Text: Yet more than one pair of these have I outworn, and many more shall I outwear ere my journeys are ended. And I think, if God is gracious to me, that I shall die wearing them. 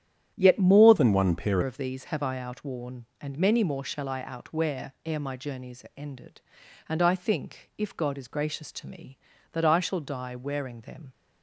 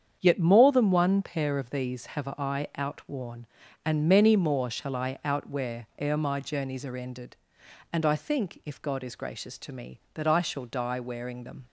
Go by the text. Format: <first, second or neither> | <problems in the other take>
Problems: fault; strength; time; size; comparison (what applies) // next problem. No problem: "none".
second | starts louder than the rest; strong; until 1.3 s; 10 dB; strong in the second // changes voice from "than" to "pair"; from 0.9 to 1.5 s; 0.6 s long